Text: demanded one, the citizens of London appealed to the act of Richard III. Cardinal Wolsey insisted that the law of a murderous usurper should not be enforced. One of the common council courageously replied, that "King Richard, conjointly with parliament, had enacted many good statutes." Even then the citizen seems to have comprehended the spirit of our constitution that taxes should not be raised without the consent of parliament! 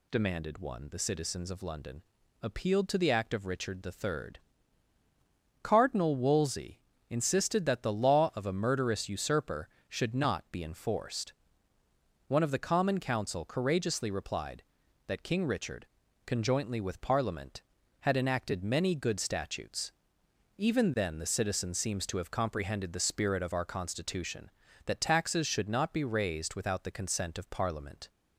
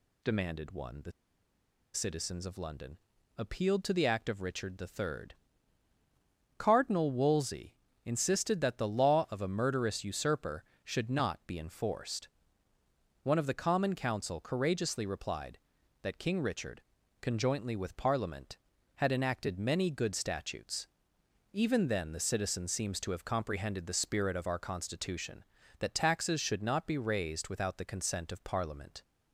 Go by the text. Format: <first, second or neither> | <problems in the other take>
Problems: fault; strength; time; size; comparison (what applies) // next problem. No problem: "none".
first | pauses between "the" and "citizens"; noticeable; at 1.1 s; 0.82 s long // pauses between "London" and "appealed"; at 2.9 s; 0.38 s long; also in the first // pauses between "Wolsey" and "insisted"; slight; at 7.7 s; 0.30 s long; slight in the first